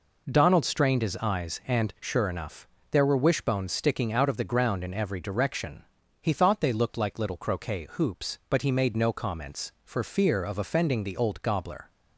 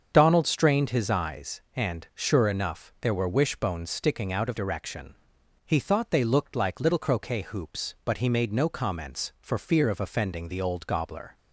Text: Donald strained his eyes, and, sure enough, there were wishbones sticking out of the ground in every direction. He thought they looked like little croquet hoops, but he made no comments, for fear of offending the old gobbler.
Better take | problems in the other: first | starts louder than the rest; until 1.1 s; 7 dB // skips "the ground in every"; at 4.5 s

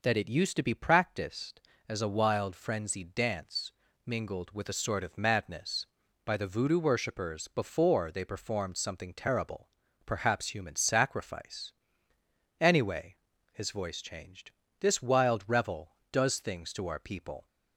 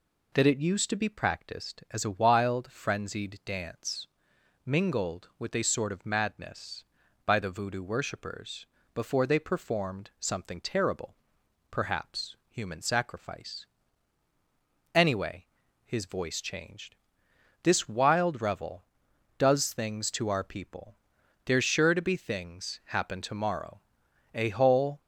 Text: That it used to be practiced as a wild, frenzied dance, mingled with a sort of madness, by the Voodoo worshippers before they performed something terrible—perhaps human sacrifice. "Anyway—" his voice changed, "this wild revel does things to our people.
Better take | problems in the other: first | pauses between "worshippers" and "before"; slight; at 8.6 s; 0.28 s long // goes on to say "There's sure to be things happen tomorrow a whole"; strong; from 21.4 s on; 3.5 s long

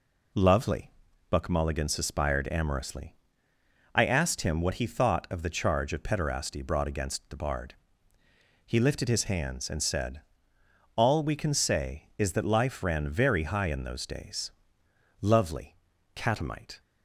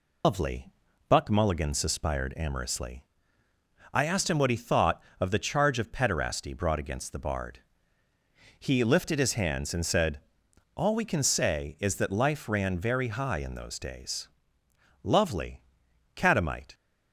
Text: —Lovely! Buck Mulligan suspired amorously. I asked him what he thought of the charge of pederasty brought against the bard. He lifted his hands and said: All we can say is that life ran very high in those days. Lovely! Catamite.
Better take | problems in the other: first | loses the start of "Lovely"; at 0.2 s; 150 ms

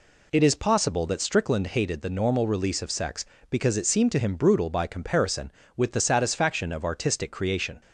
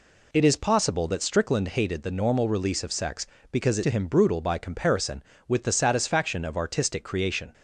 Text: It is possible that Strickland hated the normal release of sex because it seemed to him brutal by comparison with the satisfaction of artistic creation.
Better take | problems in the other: first | skips "seemed"; at 3.8 s

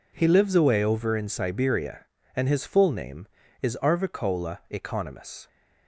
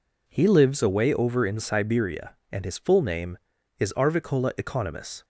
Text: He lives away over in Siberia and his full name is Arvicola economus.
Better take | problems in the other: neither | none

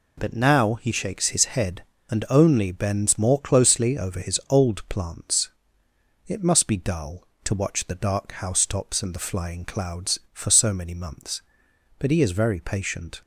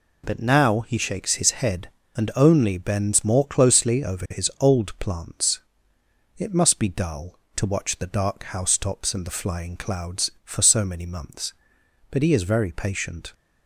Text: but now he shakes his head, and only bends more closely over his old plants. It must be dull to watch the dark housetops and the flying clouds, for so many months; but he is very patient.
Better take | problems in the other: neither | none

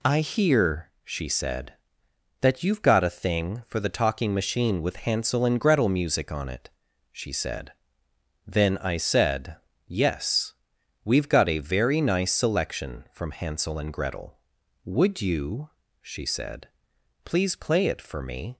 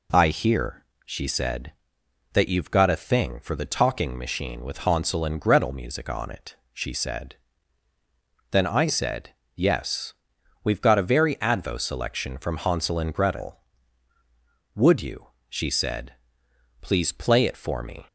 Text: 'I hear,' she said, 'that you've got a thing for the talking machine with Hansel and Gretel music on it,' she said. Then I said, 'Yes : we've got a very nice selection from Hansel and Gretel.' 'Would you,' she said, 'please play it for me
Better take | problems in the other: first | says "advo" for "nice"; at 11.3 s

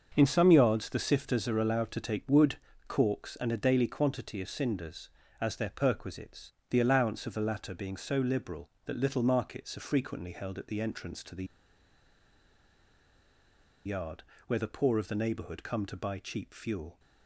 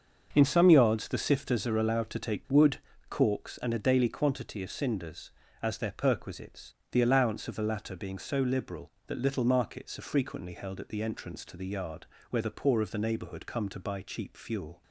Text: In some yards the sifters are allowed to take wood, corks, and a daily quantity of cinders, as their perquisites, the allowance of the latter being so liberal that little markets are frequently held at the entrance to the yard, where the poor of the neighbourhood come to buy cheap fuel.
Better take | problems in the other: second | starts louder than the rest; until 1.1 s; 7 dB; also in the second // pauses between "the" and "yard"; strong; at 11.4 s; 2.3 s long

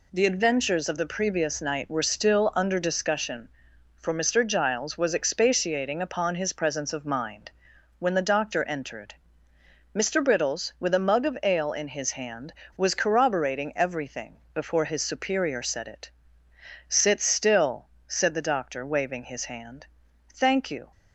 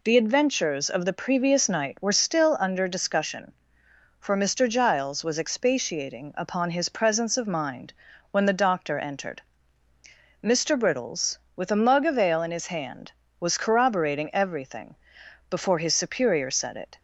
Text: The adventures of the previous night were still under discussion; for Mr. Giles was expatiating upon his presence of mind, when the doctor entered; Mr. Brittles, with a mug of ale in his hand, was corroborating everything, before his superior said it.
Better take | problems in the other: second | goes on to say "Sit still said the doctor waving his hand Thank you"; strong; from 16.8 s on; 4.0 s long

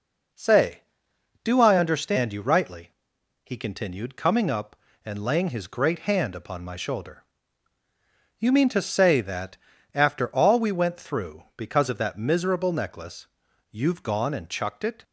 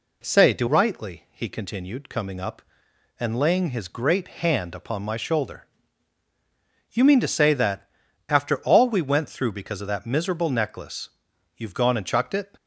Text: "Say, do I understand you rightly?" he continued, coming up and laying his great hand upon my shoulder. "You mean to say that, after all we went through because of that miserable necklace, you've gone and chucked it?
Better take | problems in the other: first | skips "I understand you"; at 0.6 s

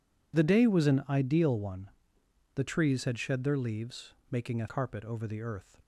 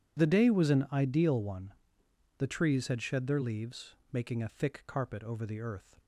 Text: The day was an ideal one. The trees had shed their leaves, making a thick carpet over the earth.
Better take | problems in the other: second | skips "thick"; at 4.6 s

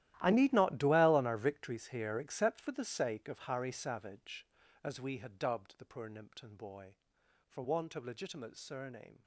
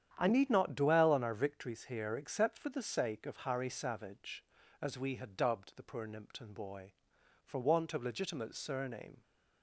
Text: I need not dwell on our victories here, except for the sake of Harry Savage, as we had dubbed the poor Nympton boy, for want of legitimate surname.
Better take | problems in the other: second | gets quieter; strong; throughout; 17 dB // starts louder than the rest; strong; until 1.2 s; 14 dB; strong in the second

